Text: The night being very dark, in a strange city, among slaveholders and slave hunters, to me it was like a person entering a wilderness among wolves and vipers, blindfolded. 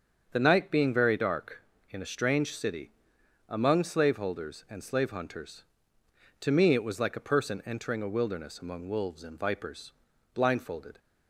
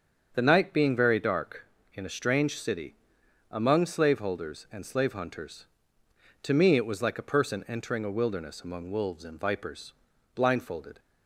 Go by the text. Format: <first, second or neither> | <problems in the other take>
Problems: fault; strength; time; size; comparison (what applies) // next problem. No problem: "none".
neither | starts louder than the rest; the same in both